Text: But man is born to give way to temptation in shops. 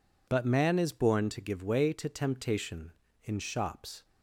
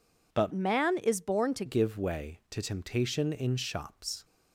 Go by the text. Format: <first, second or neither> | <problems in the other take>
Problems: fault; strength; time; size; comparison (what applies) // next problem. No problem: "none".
first | changes voice from "man" to "to"; from 0.5 to 1.6 s; 1.1 s long